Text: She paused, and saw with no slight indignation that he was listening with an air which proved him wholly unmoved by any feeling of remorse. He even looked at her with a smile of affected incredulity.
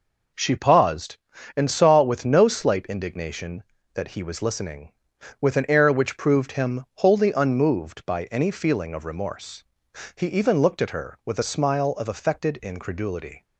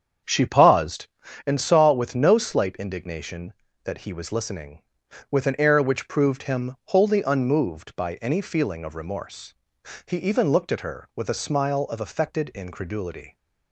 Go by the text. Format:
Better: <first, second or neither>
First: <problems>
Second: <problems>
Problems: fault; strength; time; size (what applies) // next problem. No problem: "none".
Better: first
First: none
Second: starts louder than the rest; strong; until 1.5 s; 7.5 dB